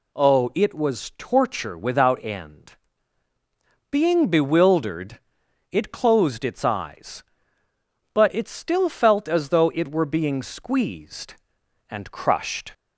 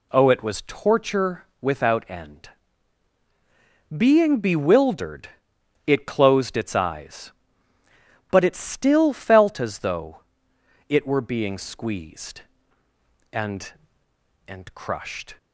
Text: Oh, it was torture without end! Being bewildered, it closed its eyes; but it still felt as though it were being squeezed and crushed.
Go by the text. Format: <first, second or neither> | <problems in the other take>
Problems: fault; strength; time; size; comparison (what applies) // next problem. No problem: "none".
first | pauses between "torture" and "without"; slight; at 1.4 s; 0.16 s long // pauses between "though" and "it"; noticeable; at 10.1 s; 0.68 s long // says "and" twice; at 14.4 s